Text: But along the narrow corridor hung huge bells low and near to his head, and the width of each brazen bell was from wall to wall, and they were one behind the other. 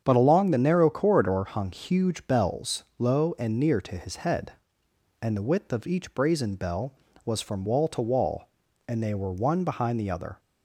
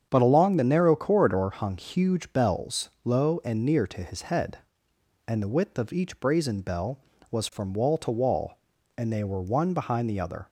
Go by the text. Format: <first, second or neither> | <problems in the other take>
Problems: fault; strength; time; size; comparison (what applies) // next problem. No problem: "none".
neither | starts louder than the rest; strong; the same in both // pauses between "bells" and "low"; slight; the same in both